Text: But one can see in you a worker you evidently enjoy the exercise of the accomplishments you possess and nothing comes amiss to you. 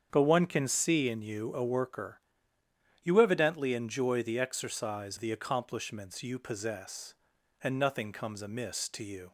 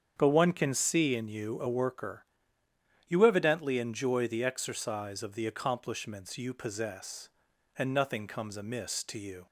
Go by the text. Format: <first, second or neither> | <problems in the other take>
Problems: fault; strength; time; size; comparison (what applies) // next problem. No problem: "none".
second | starts louder than the rest; strong; until 1.1 s; 7.5 dB; strong in the second // pauses between "worker" and "you"; noticeable; at 2.1 s; 0.84 s long; noticeable in the second // skips "of"; at 5.1 s